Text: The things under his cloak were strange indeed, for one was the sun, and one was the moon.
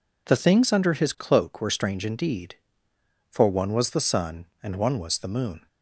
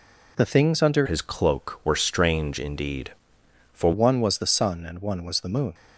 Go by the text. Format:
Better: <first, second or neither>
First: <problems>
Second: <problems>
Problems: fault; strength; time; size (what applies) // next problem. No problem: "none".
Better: first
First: none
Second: changes voice from "his" to "for"; from 1.0 to 3.9 s; 2.9 s long